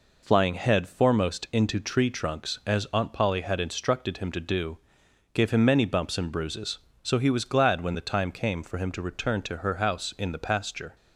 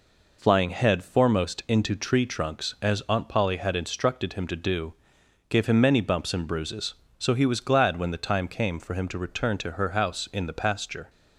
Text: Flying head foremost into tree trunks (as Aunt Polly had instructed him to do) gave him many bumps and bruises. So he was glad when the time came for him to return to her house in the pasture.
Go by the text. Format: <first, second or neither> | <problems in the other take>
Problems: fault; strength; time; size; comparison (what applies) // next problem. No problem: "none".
neither | none